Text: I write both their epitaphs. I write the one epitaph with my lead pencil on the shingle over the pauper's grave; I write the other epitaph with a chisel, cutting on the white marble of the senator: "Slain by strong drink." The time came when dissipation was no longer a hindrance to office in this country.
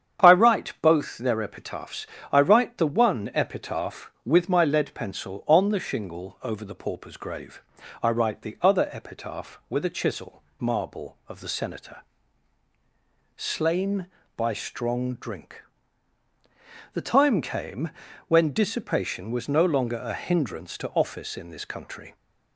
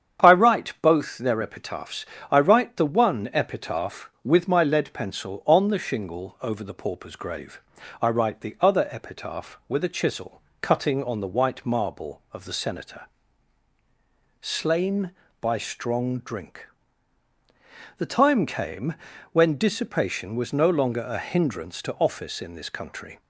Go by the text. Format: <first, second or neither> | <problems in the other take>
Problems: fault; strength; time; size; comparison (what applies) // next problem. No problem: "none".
second | starts louder than the rest; strong; until 1.3 s; 8.5 dB; strong in the second // skips "cutting on the white"; at 10.5 s // pauses between "came" and "when"; slight; at 17.9 s; 0.36 s long; slight in the second